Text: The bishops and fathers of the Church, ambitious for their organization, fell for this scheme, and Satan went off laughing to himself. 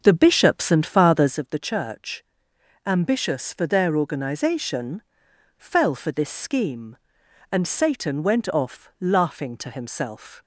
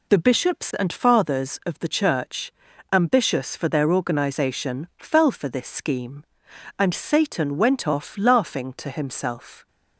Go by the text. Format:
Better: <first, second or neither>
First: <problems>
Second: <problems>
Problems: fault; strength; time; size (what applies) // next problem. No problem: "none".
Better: second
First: starts louder than the rest; until 1.4 s; 7 dB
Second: none